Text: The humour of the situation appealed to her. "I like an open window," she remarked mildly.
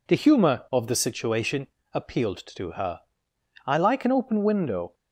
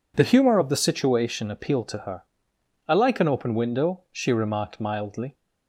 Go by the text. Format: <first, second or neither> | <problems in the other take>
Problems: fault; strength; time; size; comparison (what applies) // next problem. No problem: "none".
second | pauses between "situation" and "appealed"; slight; at 1.6 s; 0.26 s long // stops before "she remarked mildly"; at 4.9 s